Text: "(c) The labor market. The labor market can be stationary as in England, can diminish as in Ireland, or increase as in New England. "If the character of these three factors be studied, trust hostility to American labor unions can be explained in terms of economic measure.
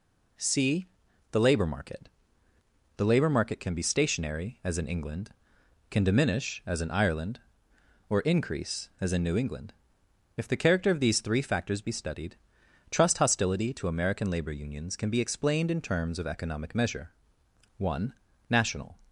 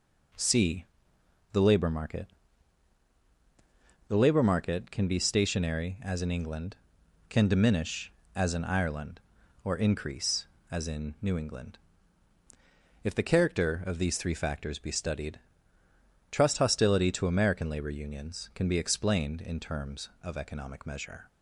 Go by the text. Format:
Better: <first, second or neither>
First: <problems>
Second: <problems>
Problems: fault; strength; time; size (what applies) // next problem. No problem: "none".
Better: second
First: goes on to say "One national"; noticeable; from 17.7 s on; 1.2 s long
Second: none